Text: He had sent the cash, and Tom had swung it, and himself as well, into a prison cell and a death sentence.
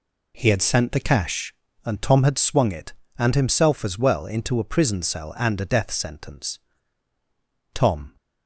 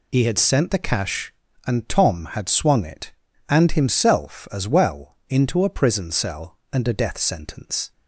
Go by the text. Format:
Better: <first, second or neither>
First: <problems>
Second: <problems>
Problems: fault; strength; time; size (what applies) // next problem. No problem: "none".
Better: second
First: goes on to say "Tom"; slight; from 7.7 s on; 0.42 s long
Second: none